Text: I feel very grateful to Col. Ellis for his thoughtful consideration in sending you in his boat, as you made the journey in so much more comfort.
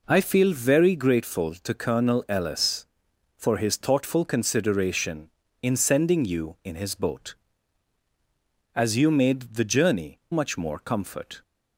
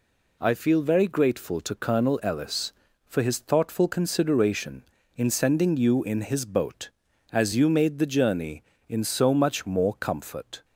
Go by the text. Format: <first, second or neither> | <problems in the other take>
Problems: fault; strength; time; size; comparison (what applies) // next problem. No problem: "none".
second | skips "in so"; at 10.2 s